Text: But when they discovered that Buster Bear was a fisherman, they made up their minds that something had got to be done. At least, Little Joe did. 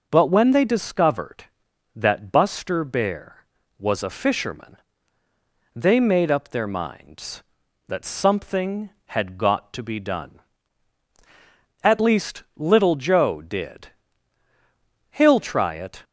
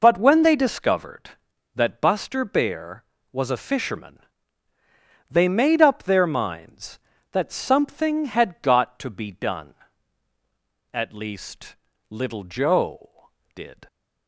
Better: second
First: goes on to say "He'll try it"; noticeable; from 15.0 s on; 0.94 s long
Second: none

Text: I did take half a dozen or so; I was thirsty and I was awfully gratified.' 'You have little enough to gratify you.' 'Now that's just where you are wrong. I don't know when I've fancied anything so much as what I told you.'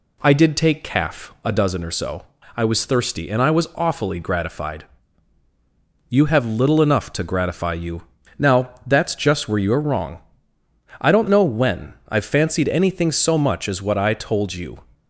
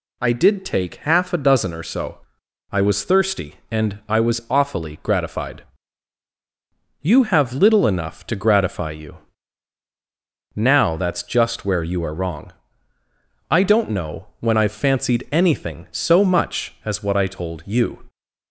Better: second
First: says "calf" for "half"; at 0.8 s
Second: none

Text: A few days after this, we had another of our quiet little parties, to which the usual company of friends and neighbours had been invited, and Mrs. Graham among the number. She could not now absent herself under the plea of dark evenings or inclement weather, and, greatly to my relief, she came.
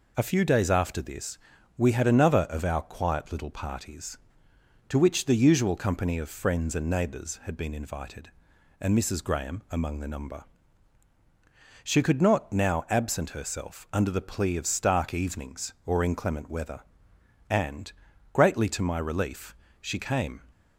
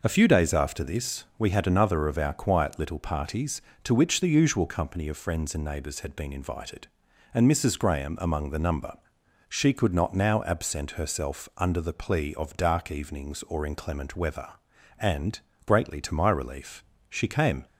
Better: second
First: says "stark" for "dark"; at 14.6 s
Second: none

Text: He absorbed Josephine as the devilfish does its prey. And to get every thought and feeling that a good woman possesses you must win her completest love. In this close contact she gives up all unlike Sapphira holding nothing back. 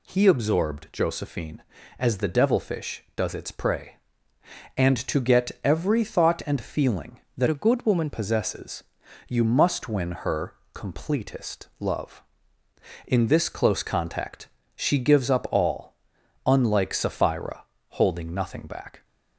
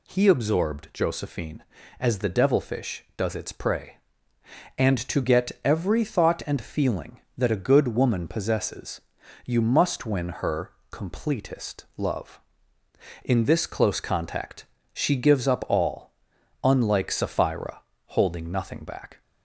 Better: second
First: changes voice from "a" to "woman"; from 7.4 to 8.0 s; 0.6 s long // pauses between "possesses" and "you"; at 8.8 s; 0.44 s long // pauses between "her" and "completest"; slight; at 10.5 s; 0.20 s long // pauses between "contact" and "she"; slight; at 14.4 s; 0.26 s long // pauses between "all" and "unlike"; noticeable; at 15.9 s; 0.52 s long // pauses between "Sapphira" and "holding"; slight; at 17.6 s; 0.26 s long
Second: pauses between "possesses" and "you"; at 9.0 s; 0.44 s long // pauses between "her" and "completest"; slight; at 10.7 s; 0.20 s long // pauses between "contact" and "she"; slight; at 14.6 s; 0.26 s long // pauses between "all" and "unlike"; noticeable; at 16.1 s; 0.52 s long // pauses between "Sapphira" and "holding"; slight; at 17.8 s; 0.26 s long

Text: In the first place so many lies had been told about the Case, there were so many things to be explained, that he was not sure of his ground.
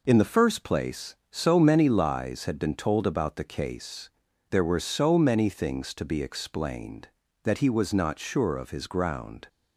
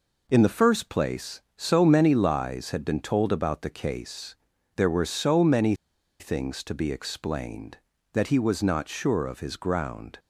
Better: first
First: none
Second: pauses between "many" and "things"; noticeable; at 5.7 s; 0.46 s long

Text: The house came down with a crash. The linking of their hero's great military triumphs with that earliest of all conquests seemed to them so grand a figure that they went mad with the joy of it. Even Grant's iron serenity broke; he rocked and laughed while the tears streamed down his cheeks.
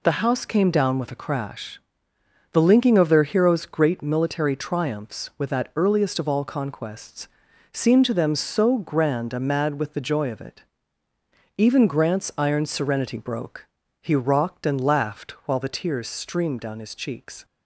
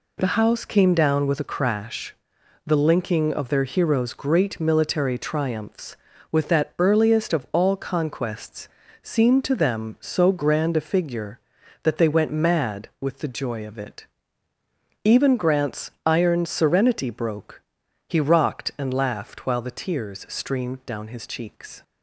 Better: second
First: pauses between "conquests" and "seemed"; at 7.2 s; 0.44 s long // skips "figure that they went"; at 9.3 s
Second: pauses between "conquests" and "seemed"; slight; at 8.6 s; 0.34 s long

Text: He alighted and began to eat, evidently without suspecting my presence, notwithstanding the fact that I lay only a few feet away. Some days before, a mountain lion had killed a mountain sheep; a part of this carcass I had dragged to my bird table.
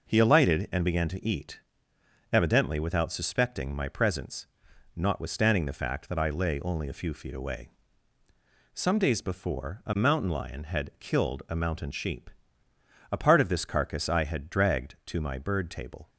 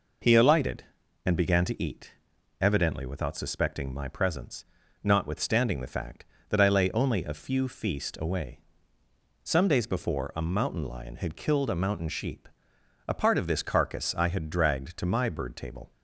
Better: first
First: none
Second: says "feast" for "feet"; at 7.6 s

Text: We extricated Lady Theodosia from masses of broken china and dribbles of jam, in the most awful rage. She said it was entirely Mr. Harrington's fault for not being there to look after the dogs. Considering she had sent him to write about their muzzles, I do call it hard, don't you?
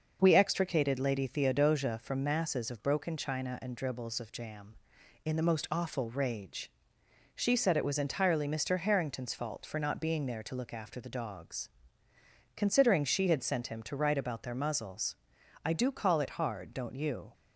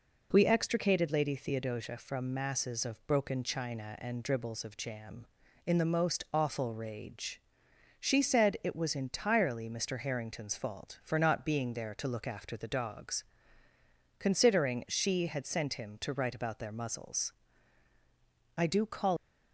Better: first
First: none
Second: stops before "it hard don't you"; at 19.1 s

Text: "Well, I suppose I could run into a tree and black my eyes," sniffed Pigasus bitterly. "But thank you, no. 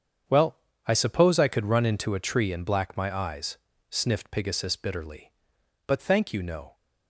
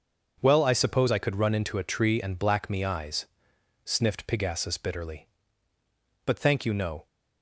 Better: first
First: starts louder than the rest; strong; until 1.5 s; 7.5 dB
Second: starts louder than the rest; noticeable; until 1.4 s; 6 dB // says "me" for "my"; at 2.6 s

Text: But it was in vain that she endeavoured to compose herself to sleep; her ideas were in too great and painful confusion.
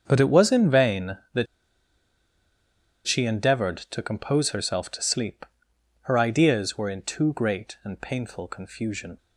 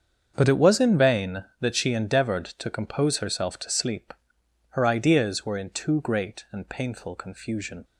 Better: second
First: starts louder than the rest; strong; until 1.0 s; 7.5 dB // pauses between "that" and "she"; strong; at 1.4 s; 1.6 s long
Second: starts louder than the rest; strong; until 1.3 s; 7.5 dB

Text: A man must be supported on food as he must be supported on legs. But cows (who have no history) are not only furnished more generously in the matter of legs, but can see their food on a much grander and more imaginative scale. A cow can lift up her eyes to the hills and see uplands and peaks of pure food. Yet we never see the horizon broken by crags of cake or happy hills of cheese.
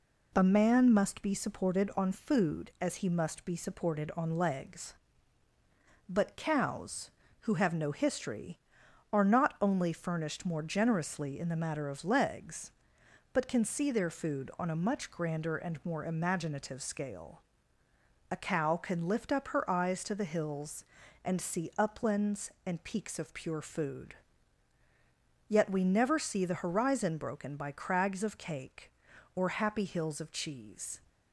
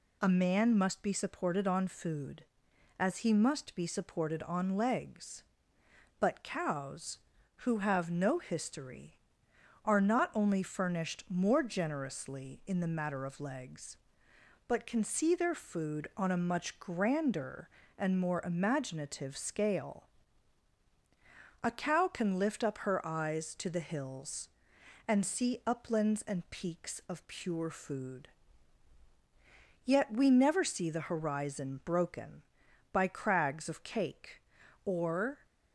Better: first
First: none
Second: stops before "happy hills of cheese"; at 35.4 s

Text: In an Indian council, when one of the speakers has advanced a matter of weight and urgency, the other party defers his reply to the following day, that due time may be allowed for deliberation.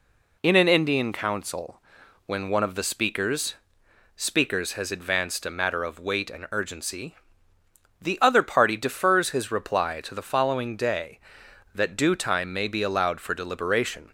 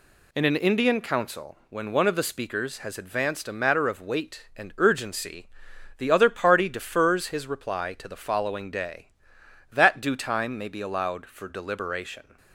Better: second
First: says "speakers" twice; at 4.1 s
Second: none

